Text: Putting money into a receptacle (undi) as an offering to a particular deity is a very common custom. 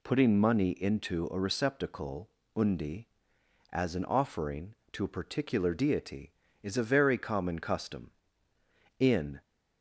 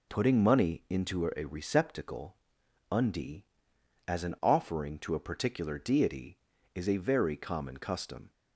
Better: second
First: goes on to say "In"; slight; from 8.9 s on; 0.44 s long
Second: none

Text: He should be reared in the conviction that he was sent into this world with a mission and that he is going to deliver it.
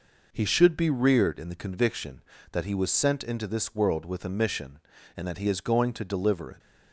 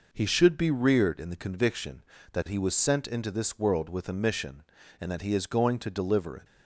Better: neither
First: none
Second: none

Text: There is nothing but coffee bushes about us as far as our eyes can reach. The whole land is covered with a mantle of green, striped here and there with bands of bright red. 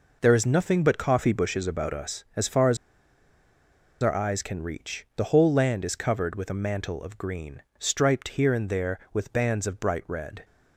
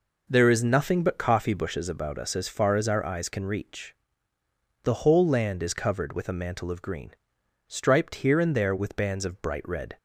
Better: second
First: pauses between "as" and "our"; strong; at 2.7 s; 1.2 s long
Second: none

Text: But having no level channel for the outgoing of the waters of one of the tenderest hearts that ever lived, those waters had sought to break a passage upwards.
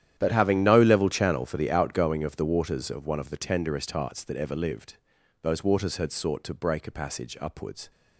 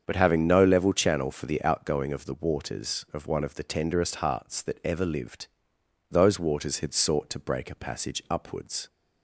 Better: second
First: gets quieter; strong; throughout; 16 dB // starts louder than the rest; strong; until 1.1 s; 10.5 dB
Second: starts louder than the rest; strong; until 1.0 s; 7 dB

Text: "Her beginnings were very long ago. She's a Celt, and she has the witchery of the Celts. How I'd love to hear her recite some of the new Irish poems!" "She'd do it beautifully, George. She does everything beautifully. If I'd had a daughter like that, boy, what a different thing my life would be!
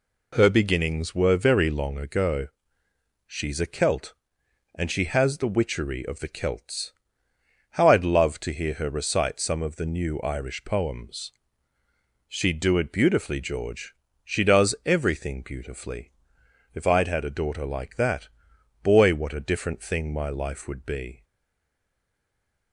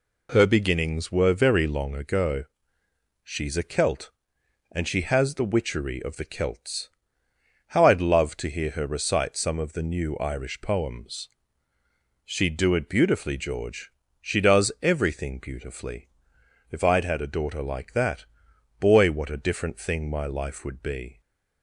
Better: second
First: stays silent after the last word; noticeable; from 21.2 s on; 1.5 s long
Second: none

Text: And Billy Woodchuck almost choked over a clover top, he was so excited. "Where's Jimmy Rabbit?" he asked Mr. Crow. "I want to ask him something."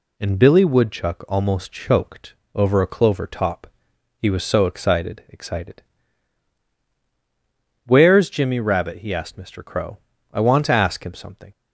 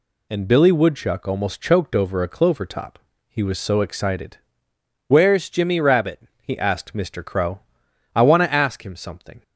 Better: second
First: pauses between "choked" and "over"; slight; at 2.3 s; 0.18 s long // says "excited" twice; at 5.2 s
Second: none

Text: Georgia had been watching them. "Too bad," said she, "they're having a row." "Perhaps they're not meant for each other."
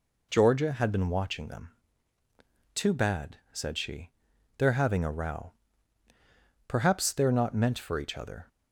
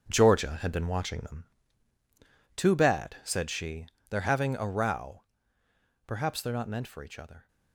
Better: first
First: none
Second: gets quieter; strong; throughout; 10.5 dB

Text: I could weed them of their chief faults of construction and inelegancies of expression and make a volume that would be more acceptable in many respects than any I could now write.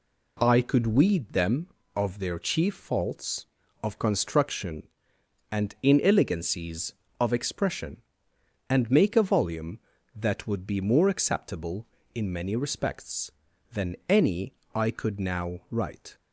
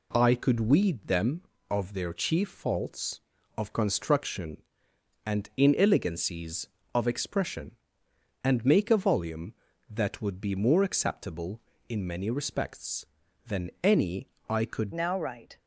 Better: first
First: pauses between "any" and "I"; slight; at 14.5 s; 0.22 s long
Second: pauses between "any" and "I"; slight; at 14.2 s; 0.22 s long // changes voice at "now"; from 14.9 s on; 0.6 s long

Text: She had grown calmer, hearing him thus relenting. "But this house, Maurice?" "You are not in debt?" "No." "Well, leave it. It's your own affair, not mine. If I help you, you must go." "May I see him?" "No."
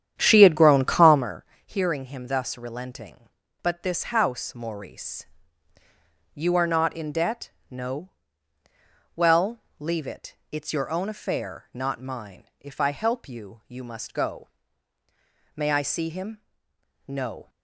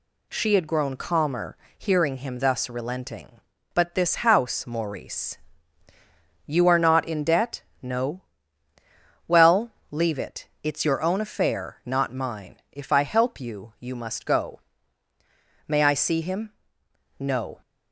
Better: second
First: starts louder than the rest; strong; until 1.3 s; 9.5 dB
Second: none

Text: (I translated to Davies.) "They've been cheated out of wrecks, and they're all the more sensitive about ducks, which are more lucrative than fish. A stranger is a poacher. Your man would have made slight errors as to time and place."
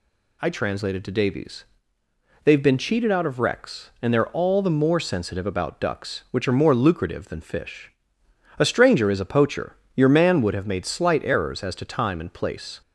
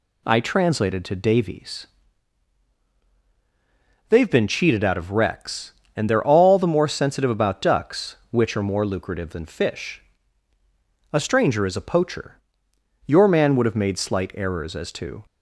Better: first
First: none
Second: stops before "time and place"; at 15.2 s

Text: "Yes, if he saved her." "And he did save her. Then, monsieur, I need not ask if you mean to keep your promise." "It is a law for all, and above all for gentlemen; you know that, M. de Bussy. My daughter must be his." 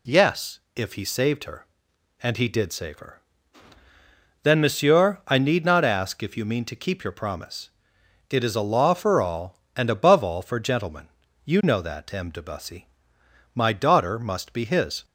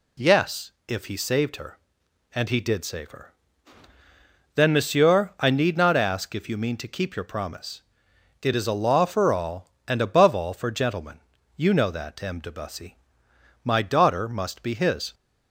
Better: neither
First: none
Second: none

